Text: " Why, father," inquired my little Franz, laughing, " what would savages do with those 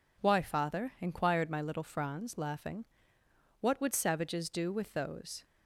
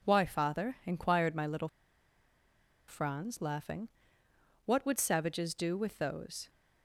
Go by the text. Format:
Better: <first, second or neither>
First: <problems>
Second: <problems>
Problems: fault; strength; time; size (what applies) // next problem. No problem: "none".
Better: first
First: none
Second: pauses between "little" and "Franz"; at 1.6 s; 1.1 s long